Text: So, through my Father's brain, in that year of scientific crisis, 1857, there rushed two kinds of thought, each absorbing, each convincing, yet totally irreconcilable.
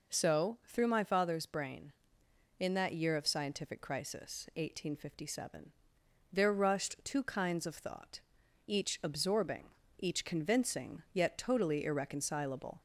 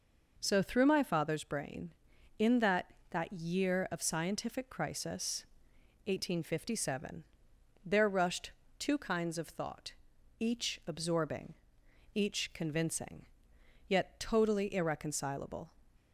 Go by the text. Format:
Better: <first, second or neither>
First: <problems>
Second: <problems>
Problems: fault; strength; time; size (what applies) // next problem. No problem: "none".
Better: first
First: none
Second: says "that" twice; at 3.0 s // pauses between "rushed" and "two"; slight; at 8.5 s; 0.26 s long